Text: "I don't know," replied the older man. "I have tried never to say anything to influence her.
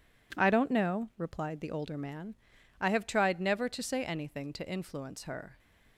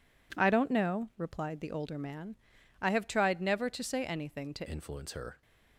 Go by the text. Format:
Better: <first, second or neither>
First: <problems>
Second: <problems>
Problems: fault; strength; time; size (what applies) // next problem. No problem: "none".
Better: first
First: none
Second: changes voice at "influence"; from 4.6 s on; 0.8 s long